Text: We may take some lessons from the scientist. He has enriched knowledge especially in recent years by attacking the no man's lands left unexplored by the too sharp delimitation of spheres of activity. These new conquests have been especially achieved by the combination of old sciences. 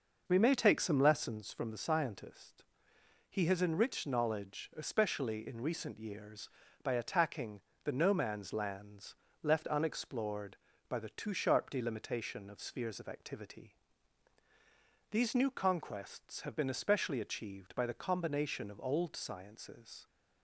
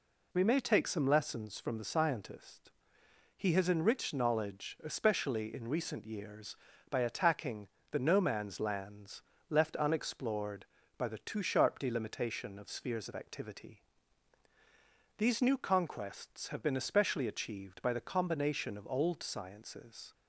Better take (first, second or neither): second